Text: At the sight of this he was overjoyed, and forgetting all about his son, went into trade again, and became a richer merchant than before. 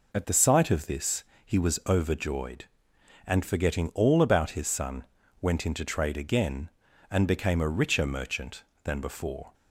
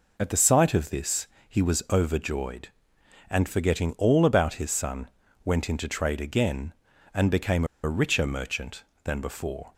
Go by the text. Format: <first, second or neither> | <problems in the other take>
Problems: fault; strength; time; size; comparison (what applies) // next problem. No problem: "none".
first | pauses between "this" and "he"; slight; at 1.2 s; 0.20 s long; slight in the first // pauses between "became" and "a"; slight; at 7.6 s; 0.19 s long